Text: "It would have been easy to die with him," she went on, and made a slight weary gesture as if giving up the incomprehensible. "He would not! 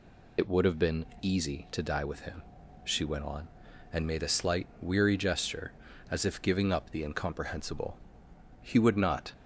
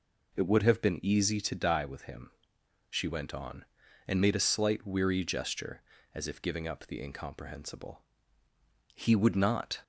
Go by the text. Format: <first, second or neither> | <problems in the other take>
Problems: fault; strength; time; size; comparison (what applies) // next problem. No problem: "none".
second | loses the start of "It"; at 0.3 s; 85 ms // pauses between "been" and "easy"; slight; at 1.0 s; 0.16 s long